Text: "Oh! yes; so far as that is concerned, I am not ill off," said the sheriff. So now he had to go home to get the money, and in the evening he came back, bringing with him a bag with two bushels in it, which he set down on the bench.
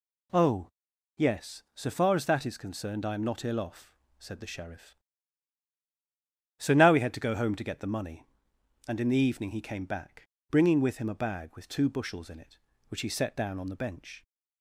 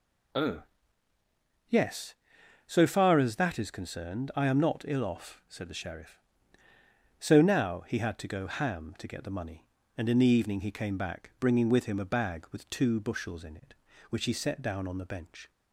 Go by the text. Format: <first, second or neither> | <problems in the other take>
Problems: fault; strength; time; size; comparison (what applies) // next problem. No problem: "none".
first | says "ham" for "home"; at 8.4 s